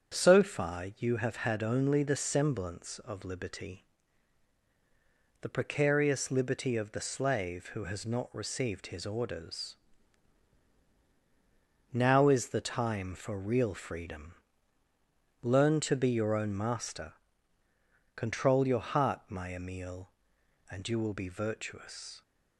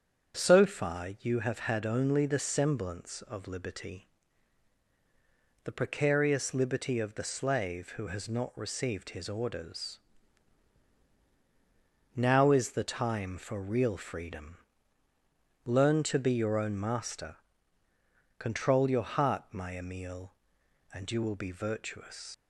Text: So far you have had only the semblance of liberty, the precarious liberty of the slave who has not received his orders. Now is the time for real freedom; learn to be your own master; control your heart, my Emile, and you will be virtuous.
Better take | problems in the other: first | starts louder than the rest; strong; until 1.4 s; 7.5 dB; strong in the first // leaves "virtuous" unfinished; at 22.3 s; 100 ms

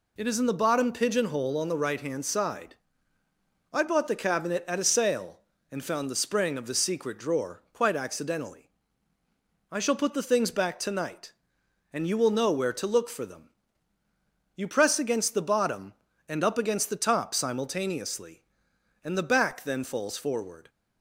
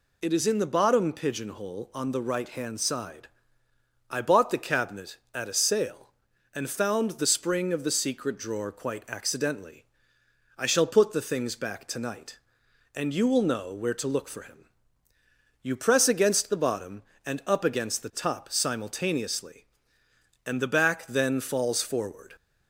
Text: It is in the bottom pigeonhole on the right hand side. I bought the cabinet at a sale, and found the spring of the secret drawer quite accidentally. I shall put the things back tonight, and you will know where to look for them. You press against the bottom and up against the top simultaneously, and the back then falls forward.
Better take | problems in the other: first | says "him" for "them"; at 14.4 s

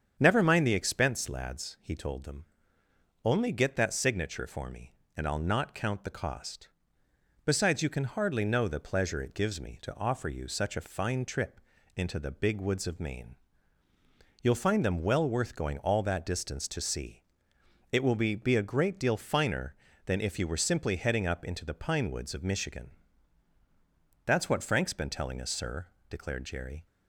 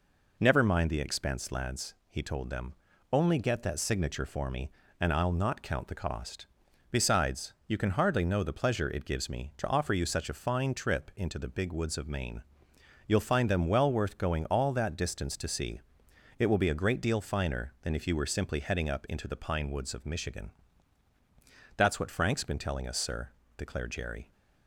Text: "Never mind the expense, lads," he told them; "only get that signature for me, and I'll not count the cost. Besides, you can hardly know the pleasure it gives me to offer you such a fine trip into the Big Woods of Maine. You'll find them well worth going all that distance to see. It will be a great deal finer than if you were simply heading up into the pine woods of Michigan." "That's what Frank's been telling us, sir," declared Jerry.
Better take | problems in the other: second | starts louder than the rest; strong; until 1.2 s; 7.5 dB // pauses between "trip" and "into"; slight; at 11.5 s; 0.36 s long // says "be" twice; at 18.3 s

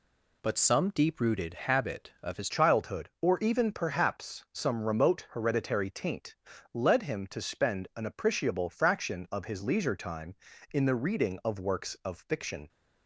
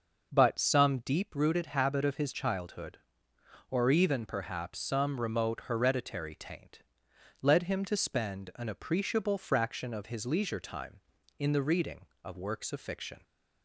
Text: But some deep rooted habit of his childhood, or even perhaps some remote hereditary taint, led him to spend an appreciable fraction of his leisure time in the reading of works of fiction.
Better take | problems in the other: second | changes voice at "childhood"; from 2.4 s on; 10.2 s long

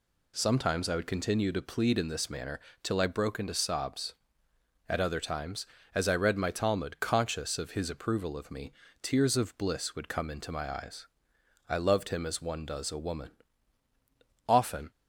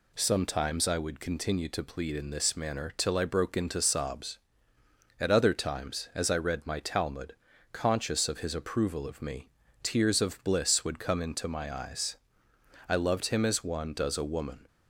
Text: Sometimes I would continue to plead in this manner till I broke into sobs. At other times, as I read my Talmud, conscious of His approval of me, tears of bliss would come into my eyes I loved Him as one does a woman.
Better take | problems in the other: second | pauses between "manner" and "till"; slight; at 2.5 s; 0.24 s long // pauses between "eyes" and "I"; noticeable; at 11.0 s; 0.62 s long; noticeable in the second // goes on to say "Often"; slight; from 14.4 s on; 0.42 s long

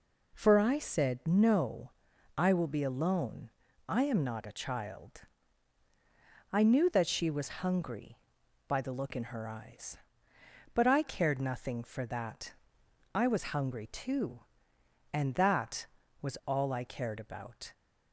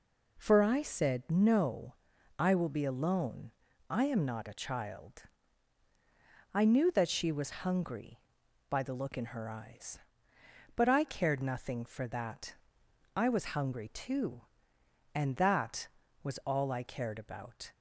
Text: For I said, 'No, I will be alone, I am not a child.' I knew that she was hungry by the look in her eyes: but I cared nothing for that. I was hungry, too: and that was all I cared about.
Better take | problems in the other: neither | none

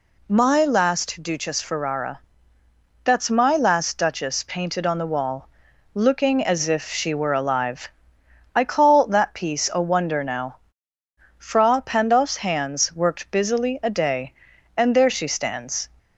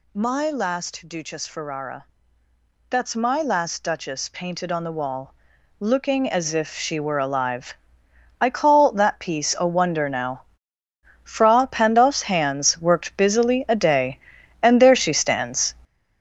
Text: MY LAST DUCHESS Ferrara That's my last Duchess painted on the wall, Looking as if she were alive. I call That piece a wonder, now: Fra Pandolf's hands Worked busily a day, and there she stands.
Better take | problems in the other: first | gets louder; strong; throughout; 8.5 dB // pauses between "Ferrara" and "That's"; noticeable; at 2.0 s; 0.84 s long; noticeable in the first

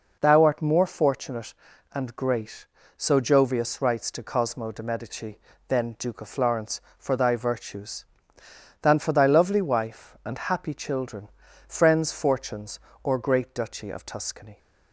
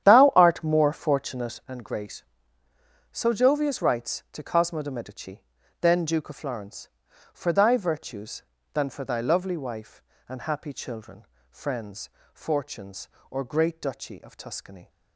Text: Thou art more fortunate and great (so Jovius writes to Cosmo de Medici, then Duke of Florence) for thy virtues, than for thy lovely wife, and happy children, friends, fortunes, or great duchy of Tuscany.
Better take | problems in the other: first | starts louder than the rest; strong; until 1.7 s; 10 dB

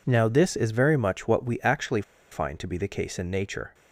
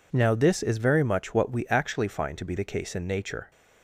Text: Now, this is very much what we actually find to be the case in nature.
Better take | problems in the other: second | pauses between "actually" and "find"; slight; at 2.0 s; 0.28 s long

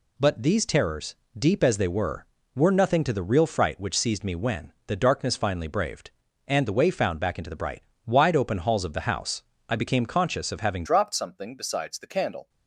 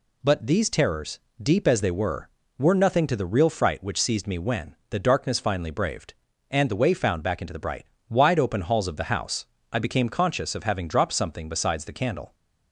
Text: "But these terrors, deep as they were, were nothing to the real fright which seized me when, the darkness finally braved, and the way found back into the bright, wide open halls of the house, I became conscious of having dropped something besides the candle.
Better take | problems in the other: second | changes voice at "dropped"; from 10.8 s on; 1.6 s long

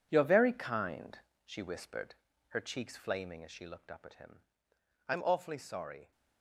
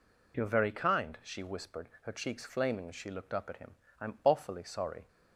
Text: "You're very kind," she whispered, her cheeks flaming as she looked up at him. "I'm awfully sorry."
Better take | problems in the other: second | gets quieter; strong; throughout; 11.5 dB

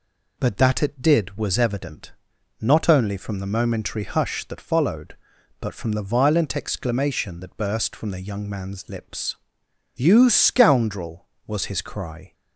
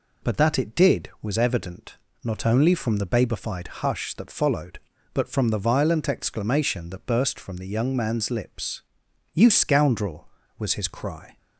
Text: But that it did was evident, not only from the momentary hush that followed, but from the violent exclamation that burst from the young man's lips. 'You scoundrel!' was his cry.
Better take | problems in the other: first | says "babified" for "momentary"; at 3.0 s

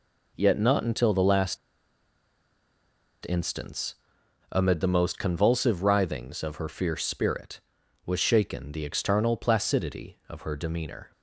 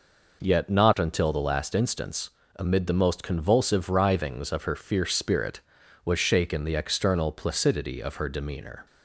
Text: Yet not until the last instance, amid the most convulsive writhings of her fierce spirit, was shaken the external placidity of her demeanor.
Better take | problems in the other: second | pauses between "last" and "instance"; strong; at 1.5 s; 1.6 s long

